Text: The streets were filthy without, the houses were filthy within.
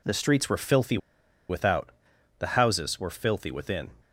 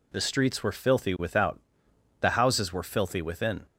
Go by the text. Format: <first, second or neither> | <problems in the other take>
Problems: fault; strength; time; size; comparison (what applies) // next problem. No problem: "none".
second | pauses between "filthy" and "without"; noticeable; at 0.9 s; 0.51 s long